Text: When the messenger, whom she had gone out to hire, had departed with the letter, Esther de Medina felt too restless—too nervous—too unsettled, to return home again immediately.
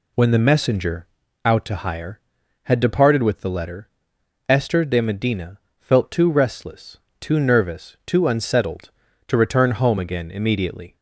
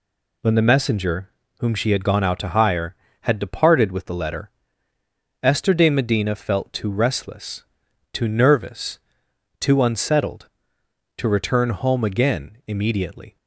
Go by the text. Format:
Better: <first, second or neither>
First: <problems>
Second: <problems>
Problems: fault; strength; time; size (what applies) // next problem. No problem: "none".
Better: second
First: skips "whom she had gone"; at 1.2 s // pauses between "Medina" and "felt"; slight; at 5.5 s; 0.20 s long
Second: none